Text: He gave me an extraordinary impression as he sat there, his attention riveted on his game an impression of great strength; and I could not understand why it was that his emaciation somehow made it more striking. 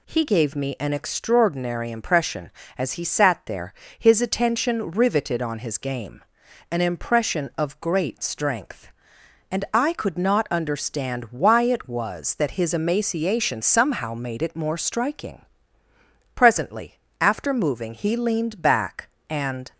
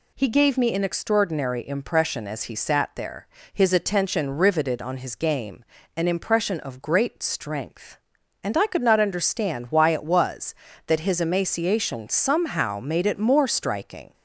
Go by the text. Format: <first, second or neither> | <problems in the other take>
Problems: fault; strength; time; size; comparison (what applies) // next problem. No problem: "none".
second | pauses between "game" and "an"; noticeable; at 6.2 s; 0.48 s long; slight in the second // goes on to say "Presently after moving he leaned back and"; strong; from 16.3 s on; 3.3 s long